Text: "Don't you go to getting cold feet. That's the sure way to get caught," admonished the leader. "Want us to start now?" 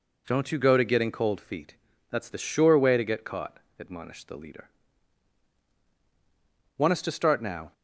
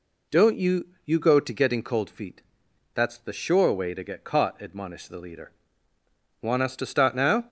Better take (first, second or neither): first